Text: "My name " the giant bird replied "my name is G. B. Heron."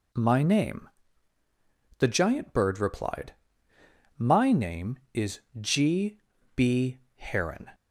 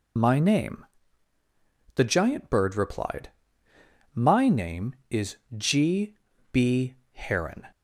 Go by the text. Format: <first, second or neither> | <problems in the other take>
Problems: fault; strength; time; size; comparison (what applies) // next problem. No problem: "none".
first | loses the start of "My"; at 0.1 s; 50 ms // pauses between "replied" and "my"; noticeable; at 3.2 s; 0.86 s long; noticeable in the first // pauses between "is" and "G"; slight; at 5.3 s; 0.22 s long; slight in the first // pauses between "G" and "B"; slight; at 6.1 s; 0.36 s long; slight in the first // pauses between "B" and "Heron"; slight; at 6.9 s; 0.16 s long; slight in the first